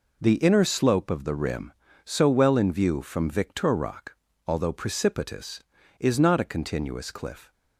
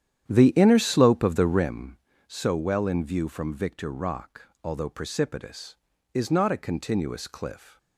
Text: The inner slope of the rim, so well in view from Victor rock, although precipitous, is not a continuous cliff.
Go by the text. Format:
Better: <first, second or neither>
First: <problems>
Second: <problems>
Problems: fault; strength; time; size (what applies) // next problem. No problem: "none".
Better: first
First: none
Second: starts louder than the rest; strong; until 1.7 s; 10 dB